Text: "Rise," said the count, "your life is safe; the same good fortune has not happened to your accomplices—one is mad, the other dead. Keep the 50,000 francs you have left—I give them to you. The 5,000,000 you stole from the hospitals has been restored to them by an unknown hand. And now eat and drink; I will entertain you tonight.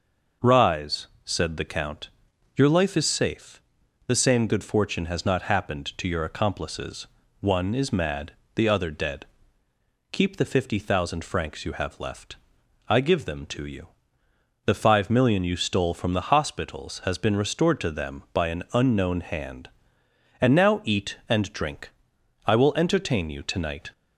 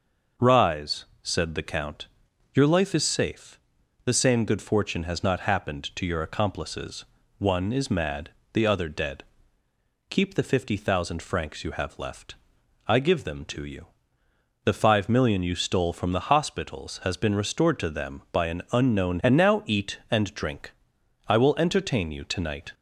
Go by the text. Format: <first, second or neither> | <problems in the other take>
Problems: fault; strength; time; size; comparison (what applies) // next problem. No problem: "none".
first | skips "hand"; at 19.2 s